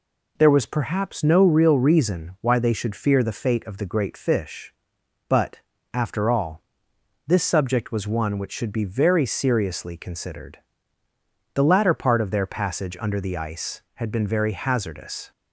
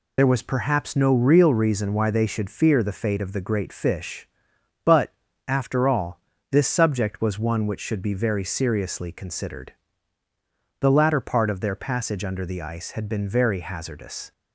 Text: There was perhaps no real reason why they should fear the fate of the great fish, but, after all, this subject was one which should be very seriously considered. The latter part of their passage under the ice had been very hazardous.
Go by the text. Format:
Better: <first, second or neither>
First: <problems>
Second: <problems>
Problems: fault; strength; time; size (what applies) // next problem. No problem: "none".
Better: first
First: none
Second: loses the start of "There"; at 0.1 s; 45 ms